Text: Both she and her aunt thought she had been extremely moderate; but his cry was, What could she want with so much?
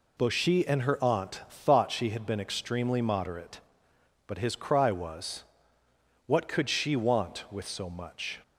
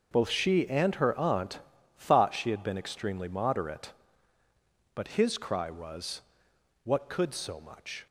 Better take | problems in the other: first | starts louder than the rest; noticeable; until 1.1 s; 6 dB // pauses between "aunt" and "thought"; at 1.6 s; 0.38 s long // skips "she want with"; at 7.3 s

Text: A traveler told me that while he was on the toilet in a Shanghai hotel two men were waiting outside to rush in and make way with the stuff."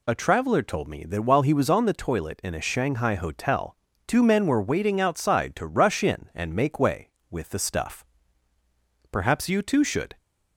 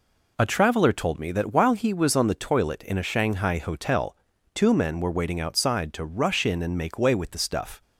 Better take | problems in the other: second | pauses between "hotel" and "two"; slight; at 3.7 s; 0.28 s long; slight in the second // goes on to say "Perhaps you too should"; noticeable; from 9.1 s on; 1.0 s long

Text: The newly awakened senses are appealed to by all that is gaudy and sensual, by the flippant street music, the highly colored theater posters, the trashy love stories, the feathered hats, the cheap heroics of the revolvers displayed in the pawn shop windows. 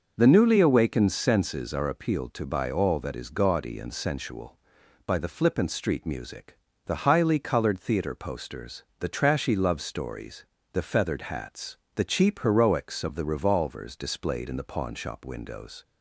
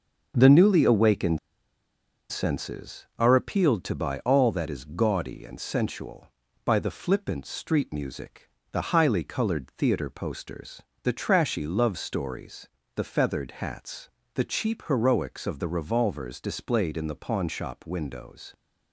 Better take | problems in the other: first | starts louder than the rest; until 1.3 s; 6.5 dB // pauses between "awakened" and "senses"; noticeable; at 1.3 s; 0.91 s long

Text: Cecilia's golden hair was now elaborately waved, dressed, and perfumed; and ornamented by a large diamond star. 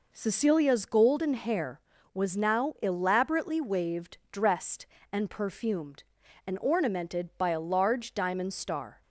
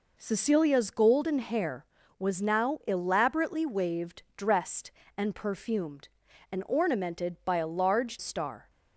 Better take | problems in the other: first | skips "diamond"; at 8.1 s

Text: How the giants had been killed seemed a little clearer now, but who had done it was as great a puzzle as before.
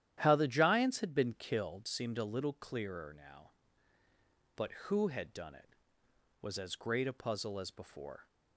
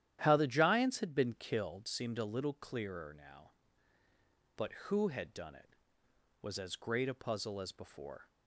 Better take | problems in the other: neither | starts louder than the rest; strong; the same in both

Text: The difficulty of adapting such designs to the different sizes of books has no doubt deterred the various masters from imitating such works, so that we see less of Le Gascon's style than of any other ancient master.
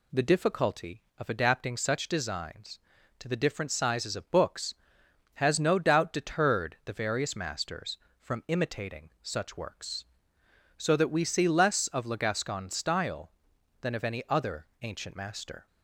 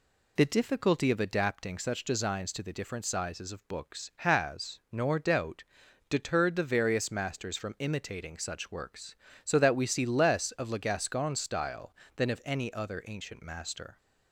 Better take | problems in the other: first | says "nor" for "no"; at 4.9 s // pauses between "doubt" and "deterred"; noticeable; at 5.6 s; 0.46 s long

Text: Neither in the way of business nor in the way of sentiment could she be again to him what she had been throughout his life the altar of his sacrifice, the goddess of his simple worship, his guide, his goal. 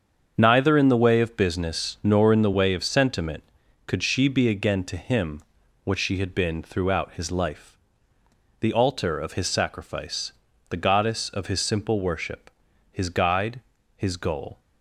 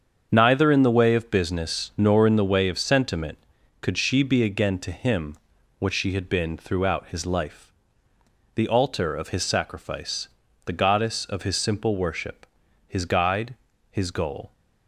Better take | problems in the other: neither | starts louder than the rest; strong; the same in both // pauses between "him" and "what"; the same in both // pauses between "life" and "the"; noticeable; the same in both

